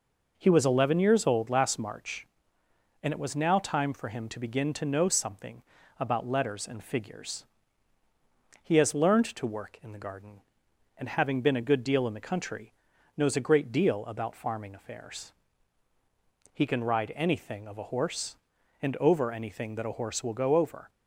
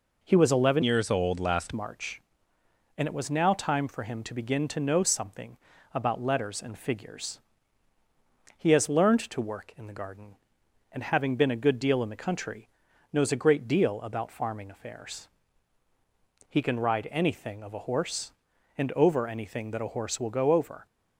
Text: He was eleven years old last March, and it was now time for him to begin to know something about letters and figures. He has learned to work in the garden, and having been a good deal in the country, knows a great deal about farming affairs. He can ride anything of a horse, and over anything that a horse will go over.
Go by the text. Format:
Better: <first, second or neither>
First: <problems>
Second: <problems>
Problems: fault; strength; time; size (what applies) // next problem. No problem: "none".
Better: first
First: pauses between "something" and "about"; slight; at 5.6 s; 0.36 s long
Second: changes voice from "years" to "last"; from 0.8 to 1.7 s; 0.9 s long // pauses between "something" and "about"; slight; at 5.5 s; 0.36 s long